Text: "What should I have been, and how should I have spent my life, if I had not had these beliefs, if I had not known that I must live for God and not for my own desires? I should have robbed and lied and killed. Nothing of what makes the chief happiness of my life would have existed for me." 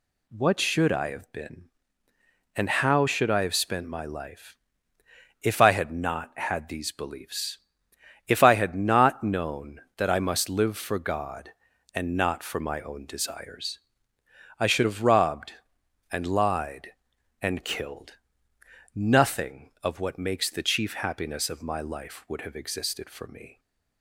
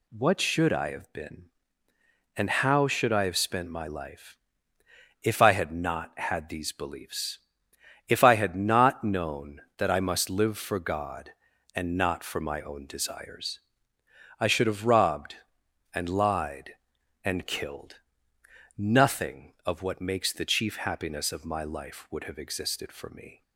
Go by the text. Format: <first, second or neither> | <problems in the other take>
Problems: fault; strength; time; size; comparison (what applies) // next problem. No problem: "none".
neither | none